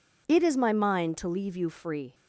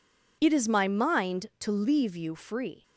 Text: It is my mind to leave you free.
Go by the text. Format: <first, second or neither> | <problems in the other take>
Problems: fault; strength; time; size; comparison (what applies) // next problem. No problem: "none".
neither | none